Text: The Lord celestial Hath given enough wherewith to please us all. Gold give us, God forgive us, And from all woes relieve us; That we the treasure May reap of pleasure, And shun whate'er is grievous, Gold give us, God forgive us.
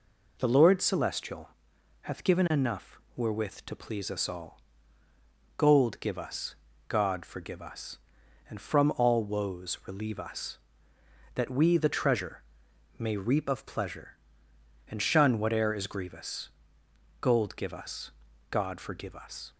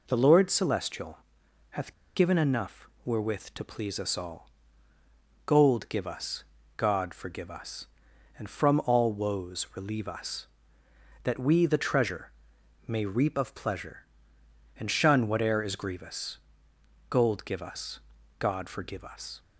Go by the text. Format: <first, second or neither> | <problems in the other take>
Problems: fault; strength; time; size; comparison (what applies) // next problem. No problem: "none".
first | pauses between "celestial" and "Hath"; noticeable; at 1.1 s; 0.50 s long; noticeable in the first // pauses between "Hath" and "given"; slight; at 1.9 s; 0.22 s long // pauses between "enough" and "wherewith"; slight; at 2.8 s; 0.16 s long; slight in the first // pauses between "treasure" and "May"; noticeable; at 12.3 s; 0.56 s long; noticeable in the first